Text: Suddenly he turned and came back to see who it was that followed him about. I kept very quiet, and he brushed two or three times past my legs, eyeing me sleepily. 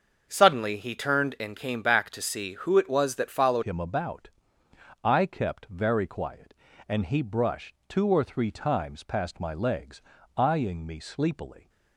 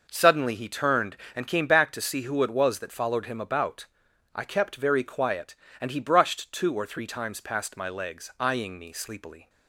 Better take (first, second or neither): second